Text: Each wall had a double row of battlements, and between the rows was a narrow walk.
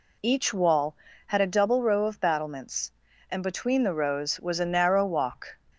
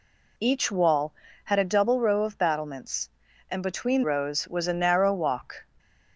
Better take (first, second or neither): first